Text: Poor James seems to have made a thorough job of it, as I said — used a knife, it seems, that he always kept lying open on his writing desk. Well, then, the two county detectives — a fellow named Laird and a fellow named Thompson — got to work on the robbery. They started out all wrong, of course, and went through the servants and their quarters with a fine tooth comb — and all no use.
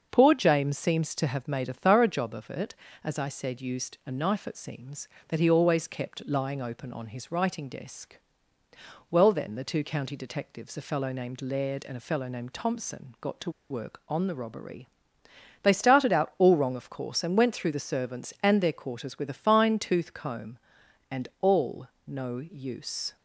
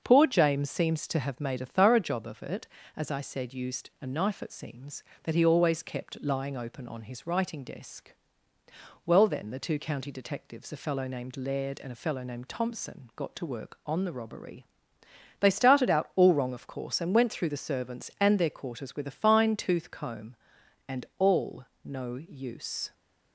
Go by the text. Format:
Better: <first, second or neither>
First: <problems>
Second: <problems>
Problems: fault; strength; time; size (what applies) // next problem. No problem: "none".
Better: second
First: starts louder than the rest; until 1.1 s; 6.5 dB // pauses between "to" and "work"; slight; at 13.4 s; 0.20 s long // pauses between "all" and "no"; slight; at 21.8 s; 0.18 s long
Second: starts louder than the rest; until 1.0 s; 6.5 dB // pauses between "all" and "no"; slight; at 21.6 s; 0.18 s long